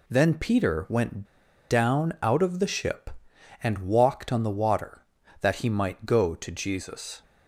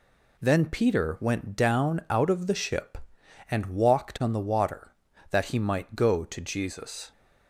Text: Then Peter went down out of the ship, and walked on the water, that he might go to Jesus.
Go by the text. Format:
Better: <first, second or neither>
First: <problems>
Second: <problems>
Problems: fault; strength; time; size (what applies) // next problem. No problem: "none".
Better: second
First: pauses between "went" and "down"; noticeable; at 1.2 s; 0.46 s long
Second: none